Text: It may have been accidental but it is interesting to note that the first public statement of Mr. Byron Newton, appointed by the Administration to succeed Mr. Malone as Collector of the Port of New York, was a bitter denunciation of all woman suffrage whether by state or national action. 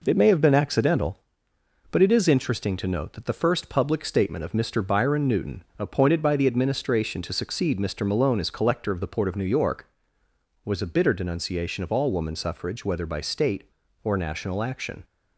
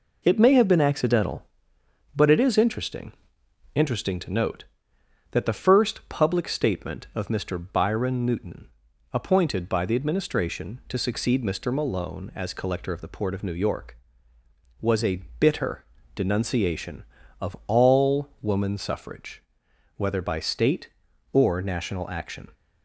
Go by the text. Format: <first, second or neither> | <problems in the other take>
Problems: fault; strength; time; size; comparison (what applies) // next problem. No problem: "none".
first | says "interesting" twice; at 3.7 s // pauses between "a" and "bitter"; slight; at 15.2 s; 0.16 s long // pauses between "bitter" and "denunciation"; slight; at 15.8 s; 0.32 s long // pauses between "suffrage" and "whether"; noticeable; at 19.4 s; 0.56 s long